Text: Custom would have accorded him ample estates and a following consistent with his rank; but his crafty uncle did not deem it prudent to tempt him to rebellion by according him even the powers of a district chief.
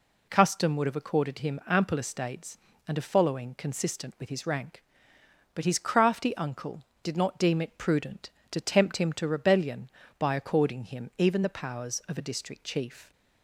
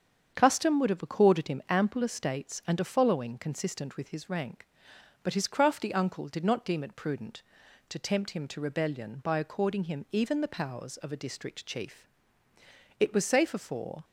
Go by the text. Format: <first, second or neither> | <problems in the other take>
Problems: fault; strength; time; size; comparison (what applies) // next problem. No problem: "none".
first | starts louder than the rest; strong; until 1.3 s; 8 dB // goes on to say "It was safer for"; noticeable; from 12.9 s on; 1.0 s long